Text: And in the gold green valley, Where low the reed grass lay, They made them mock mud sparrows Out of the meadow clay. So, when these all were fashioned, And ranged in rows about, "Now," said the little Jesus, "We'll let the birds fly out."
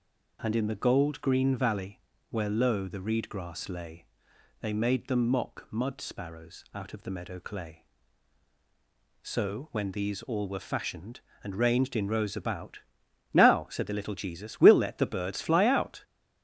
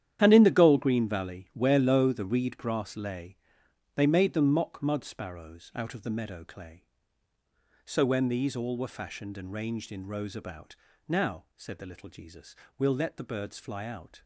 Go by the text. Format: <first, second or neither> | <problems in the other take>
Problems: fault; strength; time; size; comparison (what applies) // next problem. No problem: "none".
first | gets quieter; strong; throughout; 13 dB